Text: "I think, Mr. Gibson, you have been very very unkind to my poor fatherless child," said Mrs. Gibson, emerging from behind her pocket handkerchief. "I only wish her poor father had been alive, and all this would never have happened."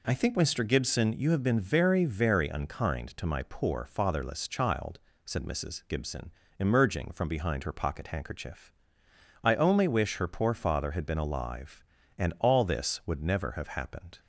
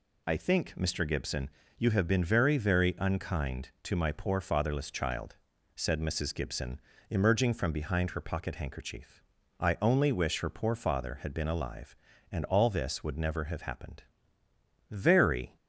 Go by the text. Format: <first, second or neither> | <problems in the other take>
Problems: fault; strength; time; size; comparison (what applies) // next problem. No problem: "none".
first | goes on to say "Very"; noticeable; from 14.9 s on; 0.64 s long